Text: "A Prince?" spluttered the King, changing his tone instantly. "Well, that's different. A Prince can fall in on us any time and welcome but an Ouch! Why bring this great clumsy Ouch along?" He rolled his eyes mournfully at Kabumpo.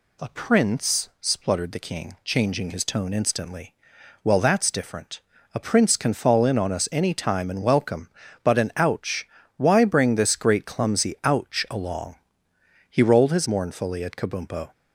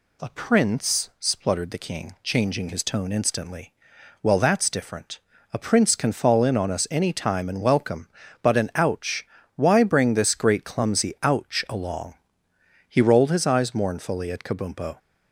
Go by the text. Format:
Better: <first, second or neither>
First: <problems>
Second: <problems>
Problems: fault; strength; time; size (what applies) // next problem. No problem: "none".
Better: second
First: skips "eyes"; at 13.4 s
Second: none